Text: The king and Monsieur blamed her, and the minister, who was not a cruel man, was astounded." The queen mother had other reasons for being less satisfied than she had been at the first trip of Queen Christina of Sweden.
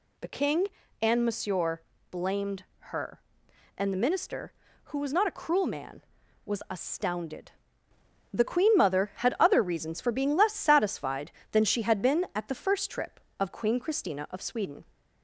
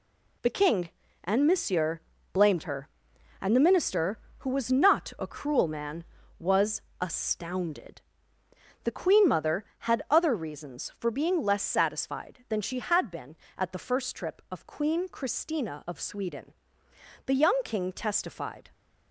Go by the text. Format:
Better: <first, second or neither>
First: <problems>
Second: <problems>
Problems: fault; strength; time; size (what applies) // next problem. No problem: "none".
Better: first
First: pauses between "Monsieur" and "blamed"; slight; at 1.8 s; 0.30 s long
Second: pauses between "Monsieur" and "blamed"; slight; at 2.0 s; 0.32 s long // pauses between "was" and "astounded"; slight; at 6.8 s; 0.20 s long // goes on to say "The young king testified"; from 17.2 s on; 1.4 s long